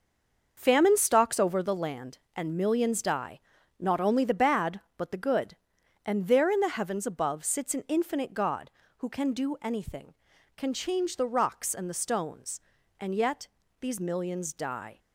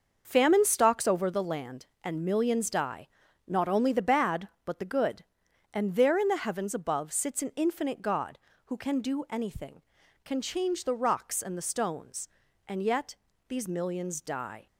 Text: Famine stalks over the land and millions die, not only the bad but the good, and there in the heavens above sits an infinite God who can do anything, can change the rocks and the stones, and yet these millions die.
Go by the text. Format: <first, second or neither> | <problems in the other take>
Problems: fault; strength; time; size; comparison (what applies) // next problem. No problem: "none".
second | stays silent before the first word; slight; until 0.5 s; 0.5 s long // starts louder than the rest; noticeable; until 1.5 s; 6 dB; noticeable in the second // pauses between "yet" and "these"; slight; at 13.4 s; 0.34 s long; slight in the second